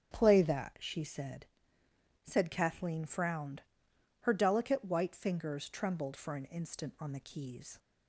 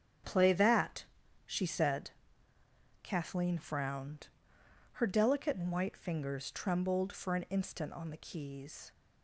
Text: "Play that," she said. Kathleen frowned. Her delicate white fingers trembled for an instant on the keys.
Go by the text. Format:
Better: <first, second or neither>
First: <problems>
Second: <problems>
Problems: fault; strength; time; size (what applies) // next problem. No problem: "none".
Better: second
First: starts louder than the rest; strong; until 1.1 s; 8.5 dB // says "said" twice; at 2.2 s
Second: starts louder than the rest; strong; until 1.6 s; 8 dB